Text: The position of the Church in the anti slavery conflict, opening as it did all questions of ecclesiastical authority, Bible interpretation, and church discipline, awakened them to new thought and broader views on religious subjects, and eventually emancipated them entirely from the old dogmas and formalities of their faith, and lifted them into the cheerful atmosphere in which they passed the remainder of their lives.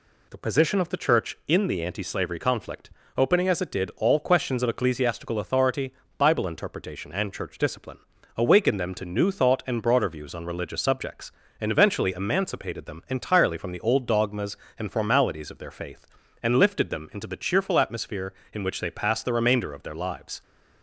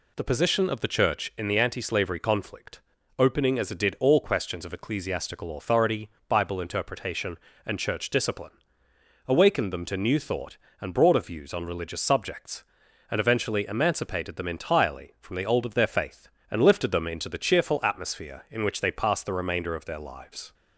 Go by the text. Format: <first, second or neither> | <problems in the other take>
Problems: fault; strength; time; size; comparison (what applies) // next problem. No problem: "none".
first | skips "dogmas and formalities"; at 15.6 s